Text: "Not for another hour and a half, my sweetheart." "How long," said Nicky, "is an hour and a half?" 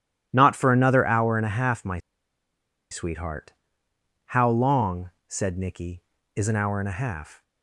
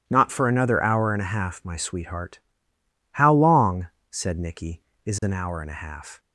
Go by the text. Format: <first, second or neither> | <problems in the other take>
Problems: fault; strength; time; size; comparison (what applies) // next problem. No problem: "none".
second | pauses between "my" and "sweetheart"; noticeable; at 1.9 s; 0.92 s long